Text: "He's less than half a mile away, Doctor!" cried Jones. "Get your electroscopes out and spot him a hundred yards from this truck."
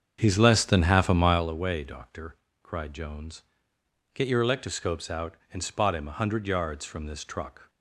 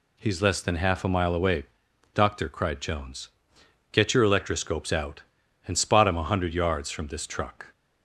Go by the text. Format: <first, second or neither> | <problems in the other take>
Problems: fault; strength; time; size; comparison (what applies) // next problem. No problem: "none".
second | starts louder than the rest; strong; until 1.5 s; 7.5 dB